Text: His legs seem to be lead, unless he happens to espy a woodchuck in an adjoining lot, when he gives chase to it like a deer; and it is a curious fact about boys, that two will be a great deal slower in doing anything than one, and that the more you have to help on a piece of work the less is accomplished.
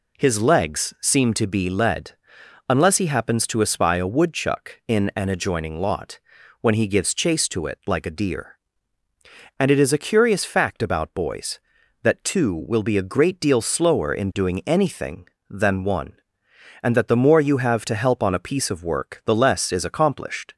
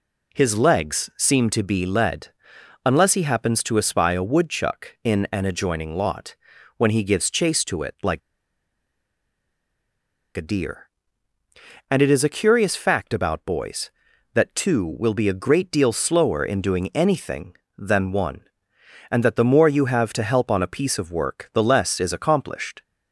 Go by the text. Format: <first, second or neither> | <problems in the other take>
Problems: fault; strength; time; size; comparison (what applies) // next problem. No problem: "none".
first | pauses between "like" and "a"; strong; at 8.2 s; 2.1 s long